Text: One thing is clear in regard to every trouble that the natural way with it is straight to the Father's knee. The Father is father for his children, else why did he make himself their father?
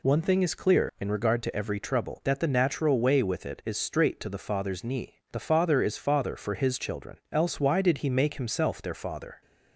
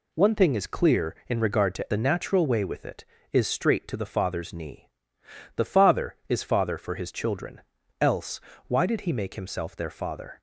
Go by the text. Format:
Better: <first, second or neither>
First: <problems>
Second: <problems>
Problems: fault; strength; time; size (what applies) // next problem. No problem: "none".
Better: first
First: none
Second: skips "every trouble that"; at 1.9 s // pauses between "else" and "why"; slight; at 8.4 s; 0.26 s long